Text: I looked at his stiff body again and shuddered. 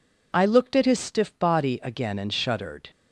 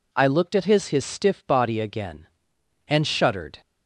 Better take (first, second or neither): first